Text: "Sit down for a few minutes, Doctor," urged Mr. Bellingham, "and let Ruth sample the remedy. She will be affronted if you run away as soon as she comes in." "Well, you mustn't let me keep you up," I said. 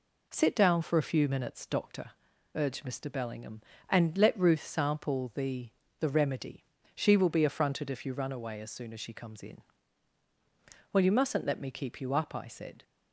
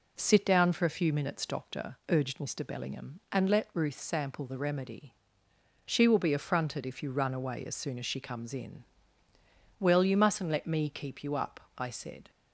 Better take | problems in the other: second | says "the" twice; at 6.0 s

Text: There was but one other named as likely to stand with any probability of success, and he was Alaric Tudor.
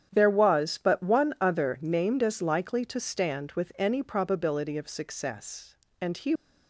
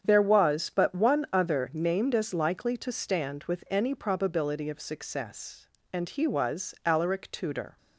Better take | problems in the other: second | starts louder than the rest; strong; until 1.1 s; 8.5 dB; strong in the second // stops before "was Alaric Tudor"; at 6.3 s

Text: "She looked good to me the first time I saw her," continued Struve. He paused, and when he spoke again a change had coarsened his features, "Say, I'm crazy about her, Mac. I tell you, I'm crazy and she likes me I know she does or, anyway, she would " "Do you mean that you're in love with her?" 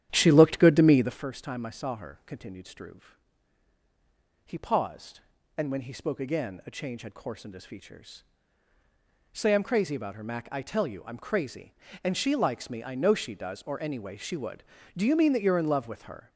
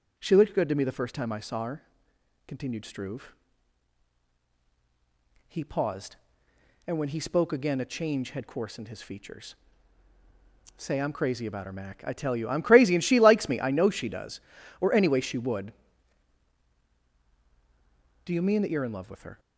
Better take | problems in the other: second | starts louder than the rest; strong; until 1.2 s; 10.5 dB

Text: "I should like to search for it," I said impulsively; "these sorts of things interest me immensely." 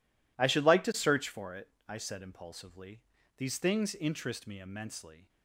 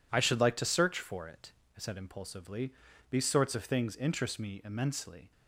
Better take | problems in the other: second | skips "sorts of"; at 3.5 s

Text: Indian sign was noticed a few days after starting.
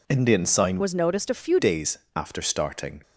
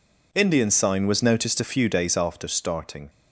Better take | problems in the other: second | changes voice from "was" to "few"; from 0.8 to 1.5 s; 0.7 s long // pauses between "days" and "after"; slight; at 1.9 s; 0.16 s long

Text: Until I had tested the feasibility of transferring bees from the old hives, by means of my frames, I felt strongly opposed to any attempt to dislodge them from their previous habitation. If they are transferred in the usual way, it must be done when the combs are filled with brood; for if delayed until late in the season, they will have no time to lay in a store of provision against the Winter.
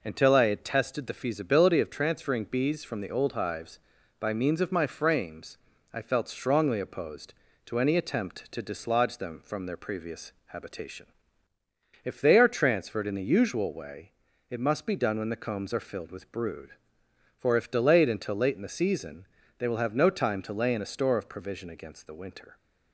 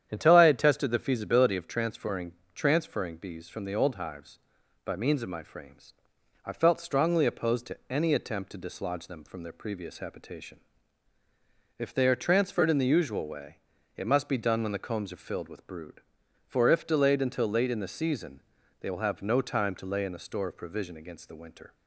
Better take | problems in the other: first | starts louder than the rest; strong; until 1.1 s; 9.5 dB // says "transferring" twice; at 2.5 s

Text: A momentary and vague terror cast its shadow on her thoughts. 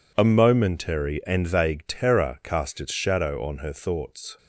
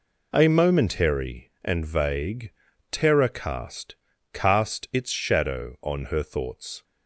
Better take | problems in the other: first | pauses between "vague" and "terror"; at 2.5 s; 0.40 s long // says "cast" twice; at 4.3 s

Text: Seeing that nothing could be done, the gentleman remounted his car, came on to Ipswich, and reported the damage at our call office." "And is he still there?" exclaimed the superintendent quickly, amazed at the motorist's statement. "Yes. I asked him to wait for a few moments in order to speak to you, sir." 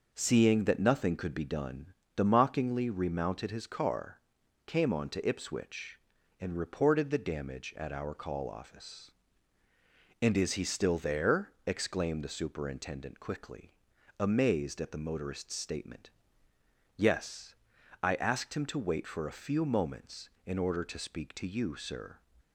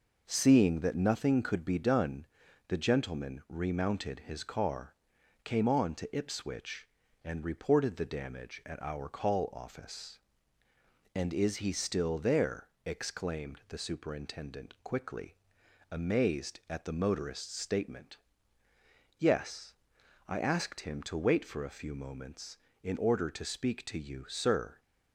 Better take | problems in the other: second | says "mockingly" for "gentleman"; at 2.2 s

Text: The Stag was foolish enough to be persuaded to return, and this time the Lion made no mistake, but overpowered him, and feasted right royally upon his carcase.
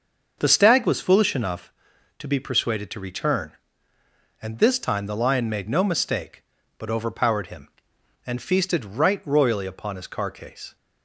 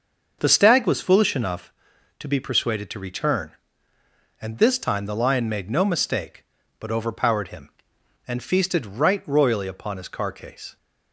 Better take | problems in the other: neither | starts louder than the rest; the same in both

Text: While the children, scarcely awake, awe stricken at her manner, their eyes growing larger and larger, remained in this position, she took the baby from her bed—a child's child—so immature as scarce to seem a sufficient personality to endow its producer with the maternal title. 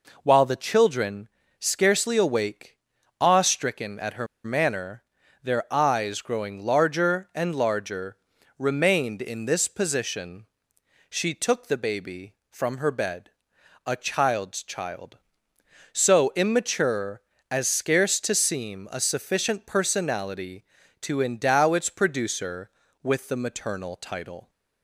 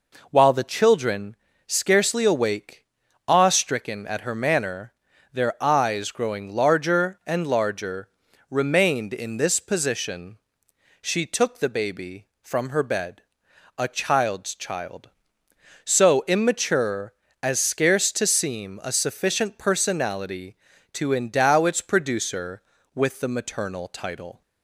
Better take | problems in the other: second | pauses between "her" and "manner"; slight; at 4.2 s; 0.18 s long

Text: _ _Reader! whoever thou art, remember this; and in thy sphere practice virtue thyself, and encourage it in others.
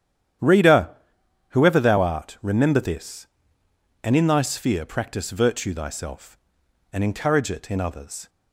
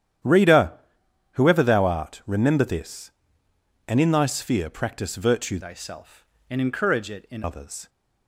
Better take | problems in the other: first | starts louder than the rest; strong; until 1.8 s; 10.5 dB; strong in the first // changes voice from "thyself" to "in"; from 5.6 to 7.4 s; 1.8 s long

